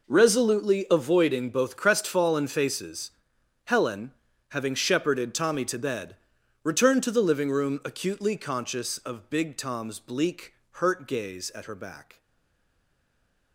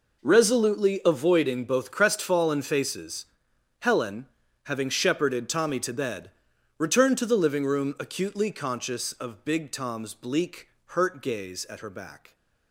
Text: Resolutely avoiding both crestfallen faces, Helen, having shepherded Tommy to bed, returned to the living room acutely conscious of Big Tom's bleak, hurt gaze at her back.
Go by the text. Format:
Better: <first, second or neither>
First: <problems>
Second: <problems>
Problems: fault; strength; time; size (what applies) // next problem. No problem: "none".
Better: second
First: stays silent after the last word; noticeable; from 12.1 s on; 1.4 s long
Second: none